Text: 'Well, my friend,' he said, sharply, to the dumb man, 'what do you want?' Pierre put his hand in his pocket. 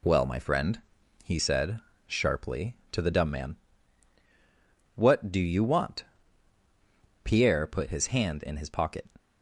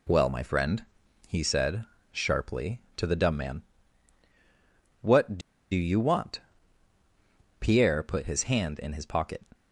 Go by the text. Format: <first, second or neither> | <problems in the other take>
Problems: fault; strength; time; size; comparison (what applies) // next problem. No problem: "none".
first | pauses between "do" and "you"; slight; at 5.4 s; 0.32 s long